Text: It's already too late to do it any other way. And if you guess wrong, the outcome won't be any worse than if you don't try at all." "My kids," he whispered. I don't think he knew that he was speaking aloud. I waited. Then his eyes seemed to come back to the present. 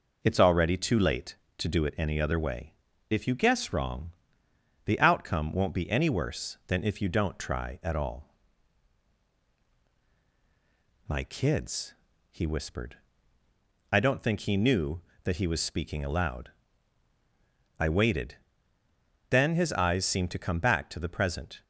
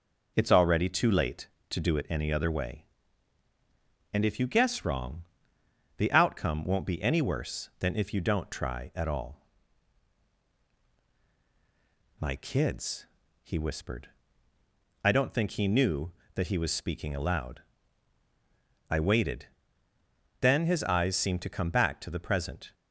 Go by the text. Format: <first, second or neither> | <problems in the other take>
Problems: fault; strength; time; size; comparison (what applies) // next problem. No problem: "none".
second | skips "And"; at 2.9 s